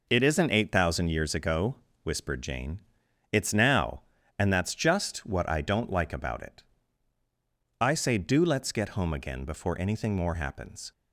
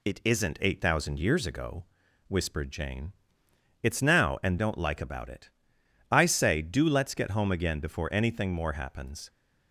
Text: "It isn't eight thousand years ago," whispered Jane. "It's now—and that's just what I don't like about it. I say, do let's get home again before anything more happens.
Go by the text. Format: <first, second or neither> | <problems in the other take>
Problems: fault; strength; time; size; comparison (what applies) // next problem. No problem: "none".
first | skips "that's just what I"; at 4.5 s